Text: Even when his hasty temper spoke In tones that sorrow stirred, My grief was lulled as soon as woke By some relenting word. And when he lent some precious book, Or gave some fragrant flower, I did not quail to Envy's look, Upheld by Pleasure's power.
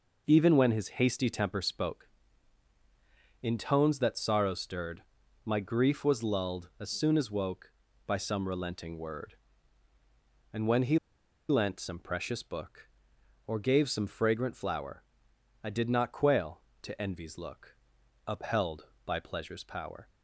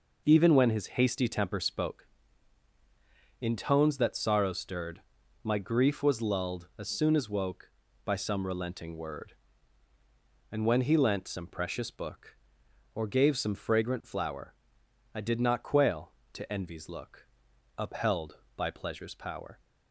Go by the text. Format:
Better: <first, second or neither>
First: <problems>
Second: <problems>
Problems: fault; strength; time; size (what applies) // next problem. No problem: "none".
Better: second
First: pauses between "he" and "lent"; noticeable; at 10.9 s; 0.52 s long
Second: none